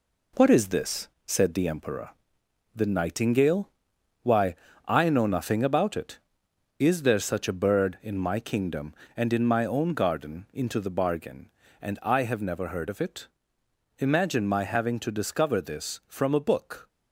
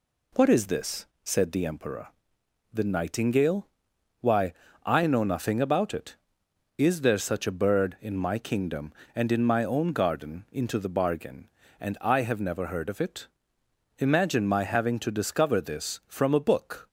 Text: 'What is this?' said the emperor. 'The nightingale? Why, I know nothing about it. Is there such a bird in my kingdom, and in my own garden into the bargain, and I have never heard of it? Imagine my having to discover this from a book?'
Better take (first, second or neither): second